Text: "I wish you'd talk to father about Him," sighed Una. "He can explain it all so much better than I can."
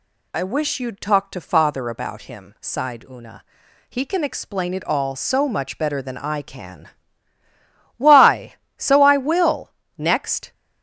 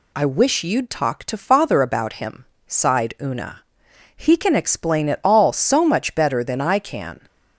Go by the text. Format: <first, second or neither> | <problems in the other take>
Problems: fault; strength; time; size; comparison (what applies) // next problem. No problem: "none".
second | goes on to say "Why so I will next"; strong; from 7.9 s on; 2.5 s long